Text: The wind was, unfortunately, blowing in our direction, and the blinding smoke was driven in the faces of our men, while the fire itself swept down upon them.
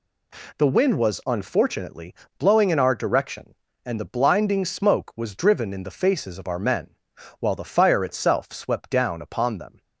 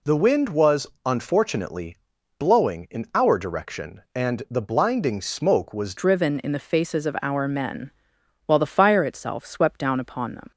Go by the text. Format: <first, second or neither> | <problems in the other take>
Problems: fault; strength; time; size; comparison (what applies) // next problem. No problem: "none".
first | changes voice at "driven"; from 5.9 s on; 4.6 s long